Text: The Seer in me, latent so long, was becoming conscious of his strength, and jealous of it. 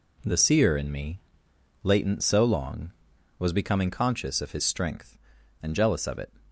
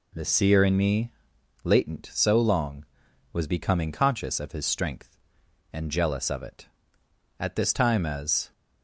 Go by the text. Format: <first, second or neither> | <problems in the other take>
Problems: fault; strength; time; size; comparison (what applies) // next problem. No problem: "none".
first | goes on to say "At this time as"; noticeable; from 7.3 s on; 1.1 s long